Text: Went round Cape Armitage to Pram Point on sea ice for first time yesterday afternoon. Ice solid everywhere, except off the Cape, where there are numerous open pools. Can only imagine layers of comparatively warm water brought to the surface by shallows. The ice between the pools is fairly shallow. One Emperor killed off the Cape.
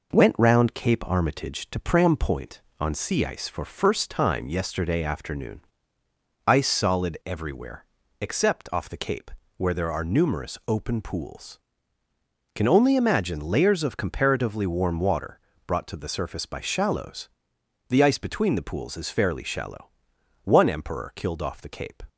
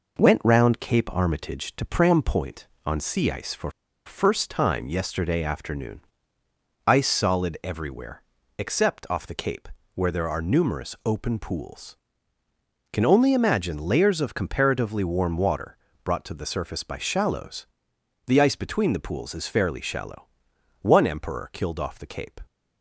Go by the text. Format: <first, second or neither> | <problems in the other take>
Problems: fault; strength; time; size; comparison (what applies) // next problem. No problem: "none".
first | pauses between "for" and "first"; at 3.6 s; 0.36 s long // pauses between "water" and "brought"; slight; at 15.7 s; 0.26 s long; slight in the first